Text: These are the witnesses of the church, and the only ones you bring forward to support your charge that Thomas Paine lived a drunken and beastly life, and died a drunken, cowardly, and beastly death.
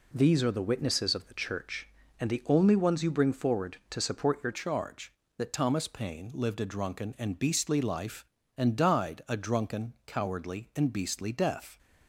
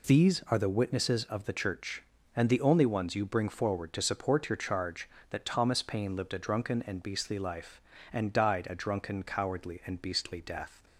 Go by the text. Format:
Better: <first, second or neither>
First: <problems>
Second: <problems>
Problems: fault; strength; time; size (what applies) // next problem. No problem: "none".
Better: second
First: changes voice at "charge"; from 4.5 s on; 7.2 s long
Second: none